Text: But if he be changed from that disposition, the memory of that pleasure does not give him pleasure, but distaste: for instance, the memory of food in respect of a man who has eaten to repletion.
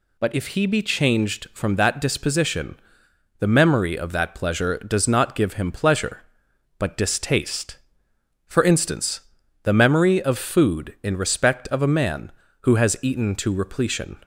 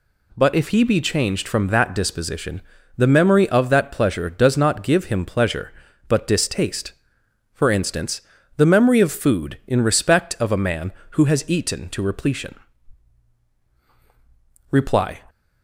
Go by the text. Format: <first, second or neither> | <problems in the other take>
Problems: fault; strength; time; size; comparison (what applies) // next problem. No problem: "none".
first | goes on to say "Reply"; from 14.6 s on; 0.52 s long